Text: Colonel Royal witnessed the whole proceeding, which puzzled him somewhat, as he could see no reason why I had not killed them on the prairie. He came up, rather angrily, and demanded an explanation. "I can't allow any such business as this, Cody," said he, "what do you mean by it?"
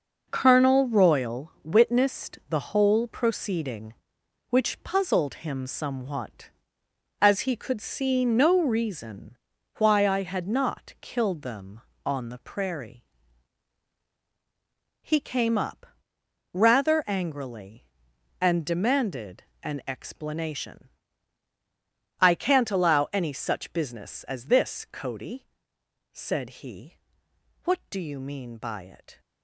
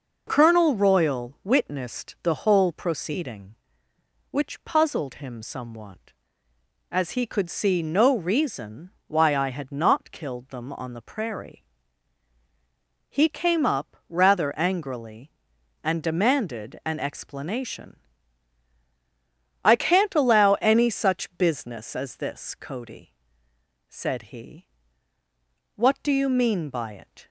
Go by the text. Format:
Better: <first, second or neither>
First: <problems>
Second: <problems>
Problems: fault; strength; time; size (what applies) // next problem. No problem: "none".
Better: second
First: gets quieter; strong; throughout; 8 dB // pauses between "reason" and "why"; at 9.3 s; 0.42 s long // pauses between "demanded" and "an"; slight; at 19.4 s; 0.18 s long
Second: pauses between "reason" and "why"; slight; at 8.9 s; 0.16 s long